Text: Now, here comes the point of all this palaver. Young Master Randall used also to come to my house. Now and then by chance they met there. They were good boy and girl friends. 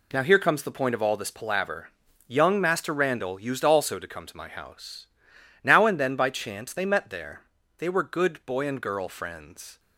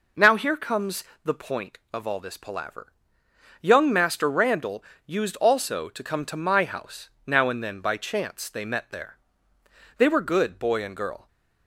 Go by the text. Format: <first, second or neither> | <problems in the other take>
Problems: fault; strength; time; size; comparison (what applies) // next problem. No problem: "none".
first | pauses between "comes" and "the"; slight; at 1.0 s; 0.18 s long // pauses between "Randall" and "used"; slight; at 4.8 s; 0.24 s long // stops before "friends"; at 11.2 s